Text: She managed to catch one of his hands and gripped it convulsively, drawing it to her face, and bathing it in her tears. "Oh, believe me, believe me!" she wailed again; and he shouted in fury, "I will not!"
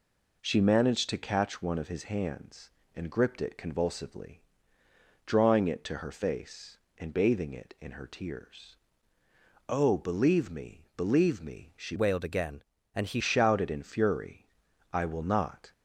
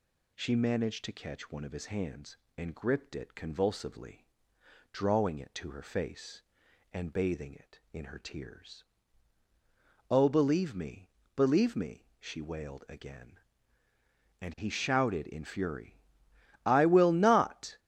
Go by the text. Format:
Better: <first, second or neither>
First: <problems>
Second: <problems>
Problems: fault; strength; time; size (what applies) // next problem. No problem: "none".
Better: second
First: changes voice from "wailed" to "he"; from 11.9 to 13.2 s; 1.3 s long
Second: none